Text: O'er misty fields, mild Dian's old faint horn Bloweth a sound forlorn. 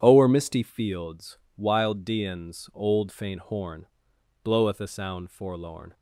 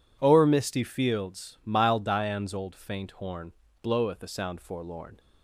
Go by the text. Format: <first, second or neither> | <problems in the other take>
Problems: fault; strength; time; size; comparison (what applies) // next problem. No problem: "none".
second | starts louder than the rest; strong; until 1.0 s; 9 dB // says "wild" for "mild"; at 1.5 s // pauses between "horn" and "Bloweth"; noticeable; at 3.8 s; 0.58 s long; slight in the second